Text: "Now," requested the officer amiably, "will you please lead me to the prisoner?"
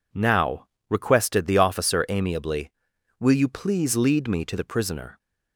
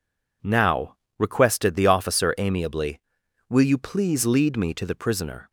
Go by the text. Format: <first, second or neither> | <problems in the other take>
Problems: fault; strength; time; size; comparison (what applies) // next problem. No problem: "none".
neither | none